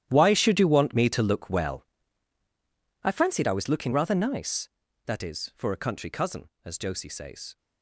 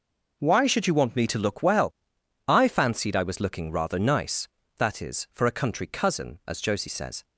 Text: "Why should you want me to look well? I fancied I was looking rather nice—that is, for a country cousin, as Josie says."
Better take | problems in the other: second | gets quieter; strong; throughout; 16.5 dB

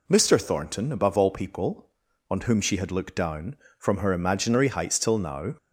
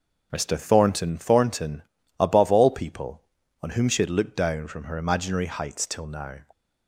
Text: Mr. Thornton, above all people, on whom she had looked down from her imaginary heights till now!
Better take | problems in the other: first | starts louder than the rest; until 1.3 s; 6.5 dB // says "Thornton" twice; at 1.1 s

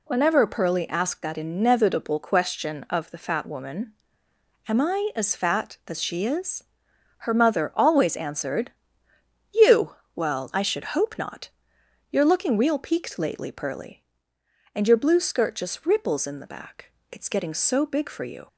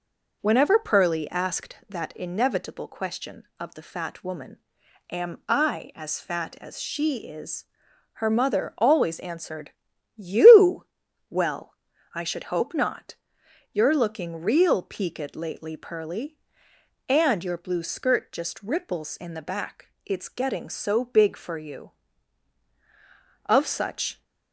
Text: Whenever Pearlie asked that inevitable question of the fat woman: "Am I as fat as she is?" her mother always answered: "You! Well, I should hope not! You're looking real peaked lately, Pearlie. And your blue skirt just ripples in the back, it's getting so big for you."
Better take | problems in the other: first | goes on to say "Of such"; noticeable; from 23.4 s on; 0.78 s long

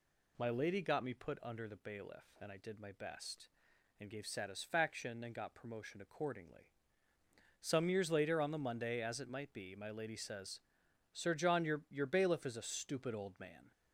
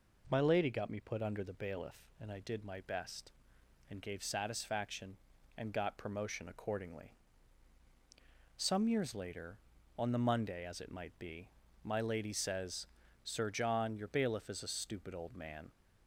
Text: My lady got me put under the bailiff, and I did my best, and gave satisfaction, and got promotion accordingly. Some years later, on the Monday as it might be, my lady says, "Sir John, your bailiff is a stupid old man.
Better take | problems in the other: second | says "your" twice; at 11.8 s

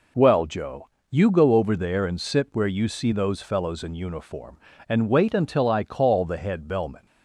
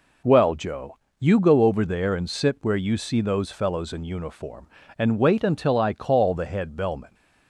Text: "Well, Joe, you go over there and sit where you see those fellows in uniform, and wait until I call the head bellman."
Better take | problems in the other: neither | none

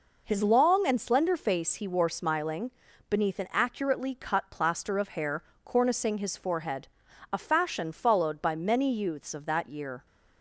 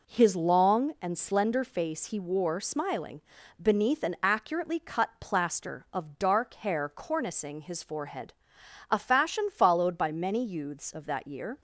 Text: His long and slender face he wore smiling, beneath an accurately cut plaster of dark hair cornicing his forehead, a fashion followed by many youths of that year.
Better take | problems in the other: second | skips "dark"; at 5.0 s // pauses between "hair" and "cornicing"; slight; at 5.4 s; 0.20 s long

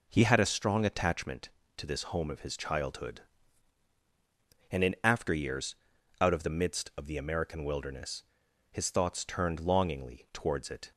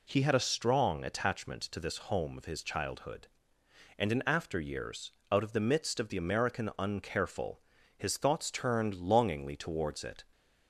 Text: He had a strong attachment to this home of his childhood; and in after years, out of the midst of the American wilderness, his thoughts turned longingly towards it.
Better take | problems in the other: first | says "uncareful" for "wilderness"; at 6.7 s

